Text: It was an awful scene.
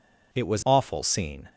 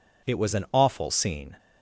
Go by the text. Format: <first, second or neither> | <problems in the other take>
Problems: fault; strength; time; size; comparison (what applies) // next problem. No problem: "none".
second | skips "an"; at 0.6 s